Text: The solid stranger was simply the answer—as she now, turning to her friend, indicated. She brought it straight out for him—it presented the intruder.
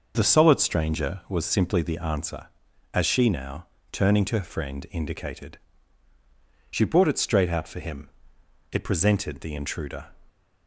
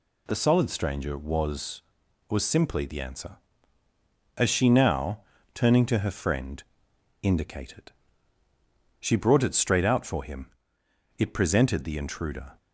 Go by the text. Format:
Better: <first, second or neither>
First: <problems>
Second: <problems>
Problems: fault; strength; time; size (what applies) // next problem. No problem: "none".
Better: first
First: none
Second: says "was" twice; at 2.2 s